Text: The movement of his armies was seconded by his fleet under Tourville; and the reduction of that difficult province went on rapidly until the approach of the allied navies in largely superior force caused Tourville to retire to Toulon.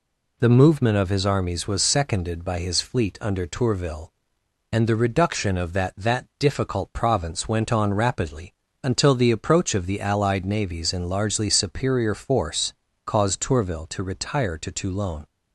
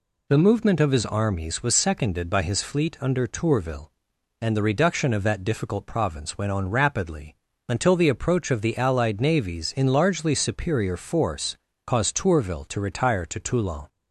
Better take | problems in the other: second | says "that" twice; at 5.9 s // pauses between "rapidly" and "until"; slight; at 8.5 s; 0.30 s long; slight in the second // pauses between "force" and "caused"; slight; at 12.7 s; 0.32 s long; slight in the second

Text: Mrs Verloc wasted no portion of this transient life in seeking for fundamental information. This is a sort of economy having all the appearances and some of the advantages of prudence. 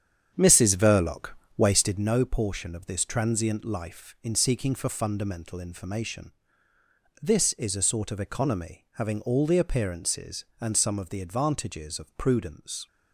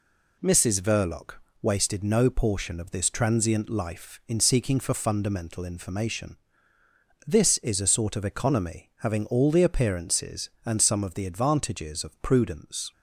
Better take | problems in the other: second | starts louder than the rest; strong; until 2.1 s; 8.5 dB // pauses between "Verloc" and "wasted"; slight; at 1.2 s; 0.30 s long; slight in the second

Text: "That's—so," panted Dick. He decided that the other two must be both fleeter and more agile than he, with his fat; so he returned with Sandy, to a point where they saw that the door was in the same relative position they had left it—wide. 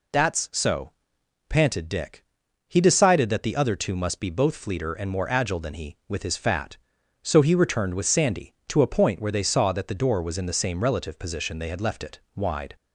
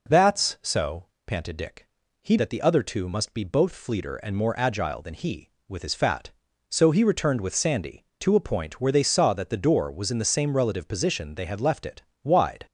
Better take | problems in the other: first | skips "decided"; at 2.3 s

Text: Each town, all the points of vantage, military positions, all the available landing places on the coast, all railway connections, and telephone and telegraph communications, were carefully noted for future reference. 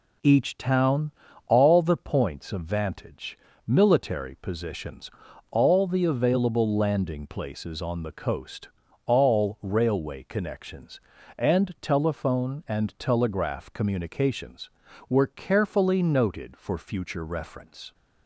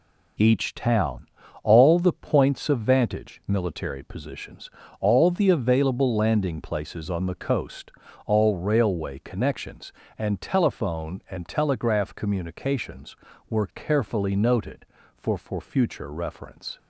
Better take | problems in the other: first | says "for" twice; at 15.3 s

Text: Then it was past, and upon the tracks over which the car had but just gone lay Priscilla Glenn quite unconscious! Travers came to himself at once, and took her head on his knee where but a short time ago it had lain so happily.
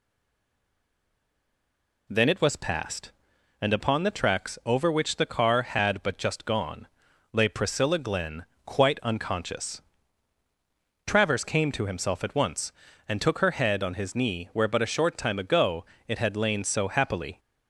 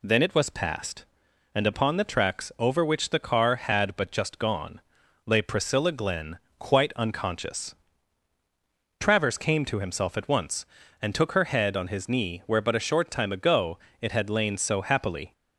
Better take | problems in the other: second | stays silent before the first word; noticeable; until 2.0 s; 2.0 s long // pauses between "gone" and "lay"; noticeable; at 6.8 s; 0.46 s long; noticeable in the second // pauses between "Glenn" and "quite"; slight; at 8.4 s; 0.20 s long; slight in the second // pauses between "ago" and "it"; slight; at 15.8 s; 0.22 s long; slight in the second

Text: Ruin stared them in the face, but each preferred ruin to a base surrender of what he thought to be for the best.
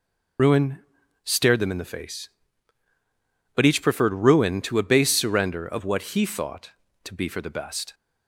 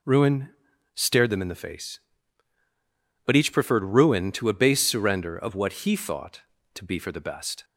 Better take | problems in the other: second | loses the start of "Ruin"; at 0.3 s; 60 ms // pauses between "Ruin" and "stared"; noticeable; at 0.7 s; 0.46 s long; noticeable in the second

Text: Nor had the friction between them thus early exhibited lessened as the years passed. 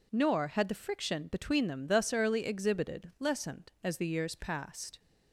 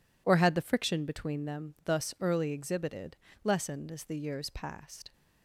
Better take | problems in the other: first | says "Or" for "Nor"; at 0.2 s // pauses between "exhibited" and "lessened"; slight; at 3.1 s; 0.26 s long

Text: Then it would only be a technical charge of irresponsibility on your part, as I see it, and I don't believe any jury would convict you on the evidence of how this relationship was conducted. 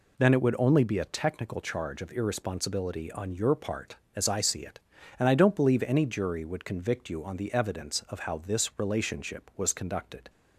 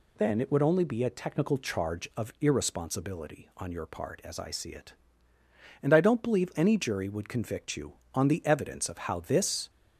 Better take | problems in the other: first | stops before "relationship was conducted"; at 9.6 s

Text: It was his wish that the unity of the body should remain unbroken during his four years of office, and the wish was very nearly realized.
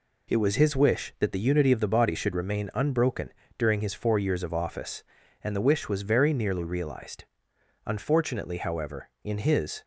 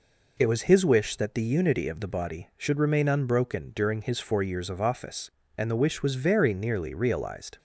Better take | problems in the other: second | pauses between "unbroken" and "during"; slight; at 3.3 s; 0.26 s long // goes on to say "Unfortunately however in his"; strong; from 7.8 s on; 1.9 s long

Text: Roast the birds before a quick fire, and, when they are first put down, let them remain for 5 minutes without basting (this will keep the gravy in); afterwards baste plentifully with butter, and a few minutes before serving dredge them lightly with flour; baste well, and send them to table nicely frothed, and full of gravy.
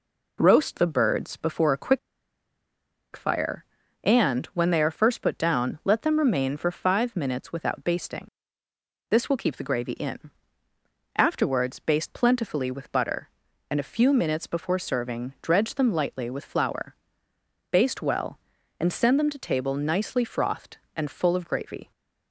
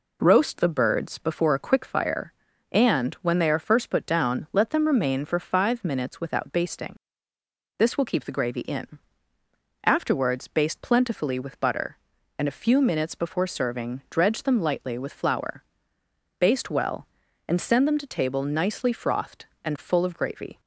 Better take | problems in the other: second | pauses between "quick" and "fire"; at 1.9 s; 1.1 s long

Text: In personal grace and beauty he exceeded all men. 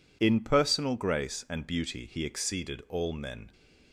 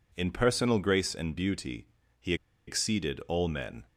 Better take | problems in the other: first | pauses between "beauty" and "he"; slight; at 1.8 s; 0.32 s long // pauses between "he" and "exceeded"; slight; at 2.3 s; 0.32 s long

